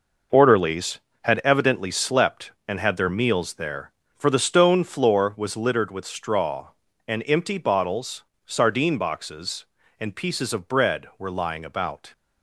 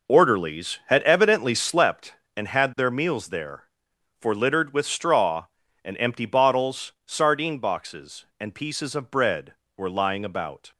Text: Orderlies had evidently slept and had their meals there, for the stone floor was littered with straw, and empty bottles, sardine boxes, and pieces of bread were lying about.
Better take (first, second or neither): first